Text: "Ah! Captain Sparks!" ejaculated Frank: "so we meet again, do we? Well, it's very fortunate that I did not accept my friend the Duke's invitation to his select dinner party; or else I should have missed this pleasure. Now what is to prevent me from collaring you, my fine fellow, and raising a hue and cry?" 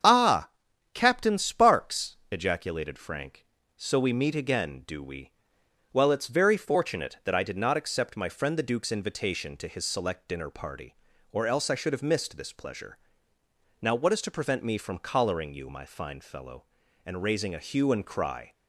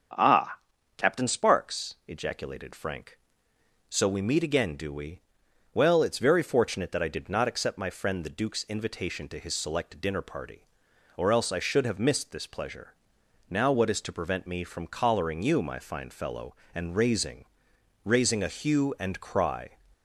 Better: first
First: starts louder than the rest; strong; until 1.5 s; 8 dB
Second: starts louder than the rest; strong; until 1.5 s; 7 dB // says "raising" twice; at 18.0 s

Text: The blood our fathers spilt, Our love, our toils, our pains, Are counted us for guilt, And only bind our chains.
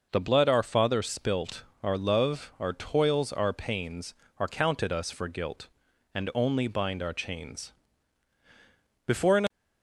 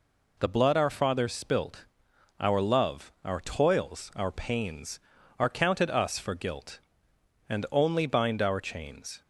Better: second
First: goes on to say "Before an"; slight; from 9.0 s on; 0.44 s long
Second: none

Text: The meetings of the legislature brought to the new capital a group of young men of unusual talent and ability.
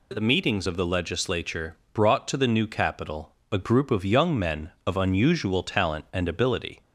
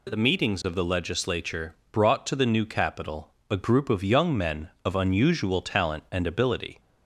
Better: neither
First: pauses between "legislature" and "brought"; slight; at 1.7 s; 0.16 s long // pauses between "capital" and "a"; slight; at 3.3 s; 0.16 s long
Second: pauses between "legislature" and "brought"; slight; at 1.7 s; 0.16 s long // pauses between "capital" and "a"; slight; at 3.3 s; 0.16 s long

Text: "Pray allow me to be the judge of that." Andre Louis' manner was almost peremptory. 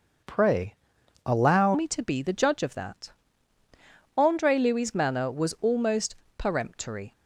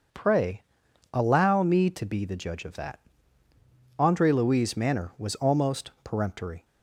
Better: second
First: pauses between "Pray" and "allow"; noticeable; at 0.7 s; 0.52 s long // changes voice at "me"; from 1.7 s on; 5.4 s long // pauses between "almost" and "peremptory"; slight; at 6.1 s; 0.22 s long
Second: pauses between "Pray" and "allow"; noticeable; at 0.6 s; 0.52 s long

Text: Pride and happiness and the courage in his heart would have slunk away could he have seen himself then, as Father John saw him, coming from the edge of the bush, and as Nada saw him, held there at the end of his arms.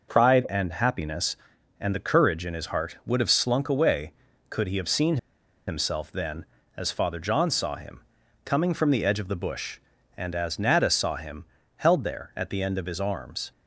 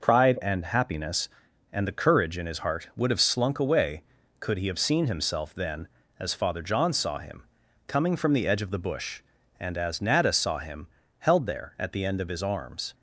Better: second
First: pauses between "seen" and "himself"; noticeable; at 5.1 s; 0.50 s long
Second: none

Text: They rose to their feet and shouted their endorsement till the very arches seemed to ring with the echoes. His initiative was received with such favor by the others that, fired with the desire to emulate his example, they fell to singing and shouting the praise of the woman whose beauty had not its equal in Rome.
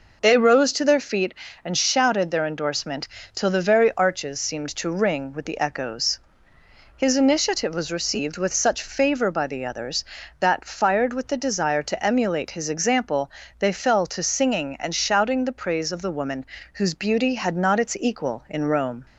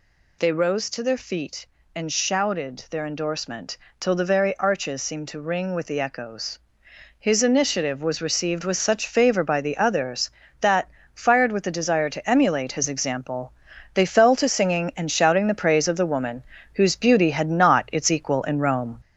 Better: first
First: pauses between "endorsement" and "till"; slight; at 3.0 s; 0.28 s long // pauses between "woman" and "whose"; slight; at 16.4 s; 0.28 s long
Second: gets louder; slight; throughout; 3 dB // pauses between "endorsement" and "till"; slight; at 3.7 s; 0.22 s long // pauses between "woman" and "whose"; slight; at 16.4 s; 0.30 s long

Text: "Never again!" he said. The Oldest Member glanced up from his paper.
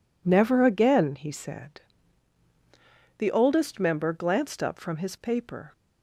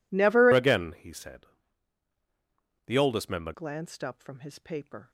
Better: first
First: none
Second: changes voice from "again" to "Member"; from 0.5 to 3.5 s; 3.0 s long

